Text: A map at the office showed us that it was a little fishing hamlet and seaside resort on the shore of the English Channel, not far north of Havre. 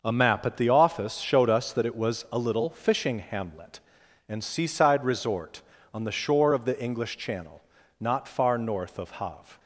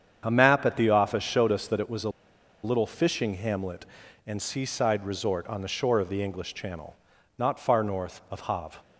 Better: first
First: starts louder than the rest; noticeable; until 1.0 s; 6 dB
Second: starts louder than the rest; strong; until 1.2 s; 8 dB // pauses between "a" and "little"; noticeable; at 2.0 s; 0.53 s long

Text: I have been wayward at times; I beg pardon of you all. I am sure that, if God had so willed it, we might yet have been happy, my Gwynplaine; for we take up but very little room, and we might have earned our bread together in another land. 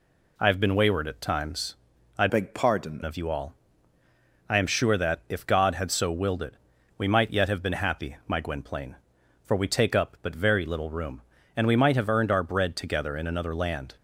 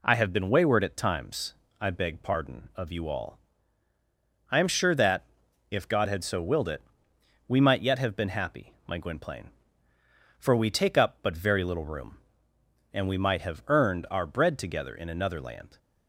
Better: second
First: changes voice from "beg" to "pardon"; from 2.2 to 3.0 s; 0.8 s long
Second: none

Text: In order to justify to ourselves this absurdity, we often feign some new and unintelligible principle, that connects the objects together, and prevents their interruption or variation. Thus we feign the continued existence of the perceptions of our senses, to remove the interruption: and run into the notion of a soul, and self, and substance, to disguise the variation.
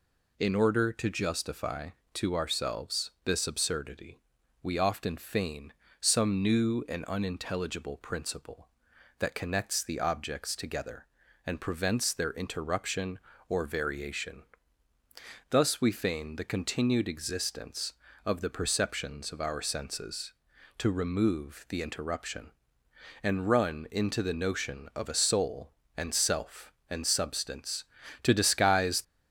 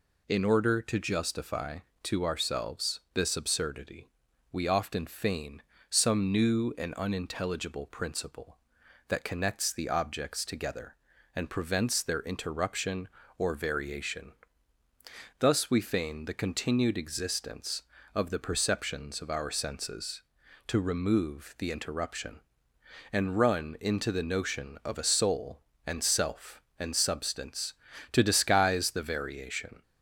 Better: second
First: pauses between "feign" and "some"; slight; at 5.7 s; 0.30 s long // stops before "the variation"; at 29.0 s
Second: pauses between "feign" and "some"; slight; at 5.6 s; 0.30 s long

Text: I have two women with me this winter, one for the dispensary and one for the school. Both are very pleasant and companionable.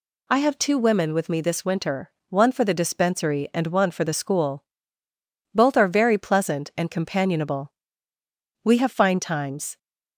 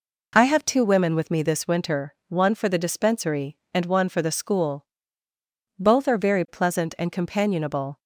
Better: second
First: goes on to say "We have fine times"; noticeable; from 8.6 s on; 1.1 s long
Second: none

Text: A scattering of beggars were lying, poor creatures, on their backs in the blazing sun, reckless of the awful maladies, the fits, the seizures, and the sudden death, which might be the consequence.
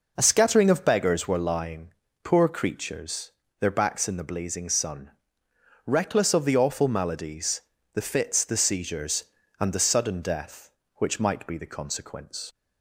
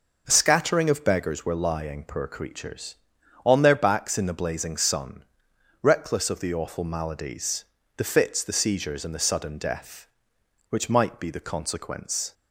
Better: second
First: skips "on"; at 3.4 s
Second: none

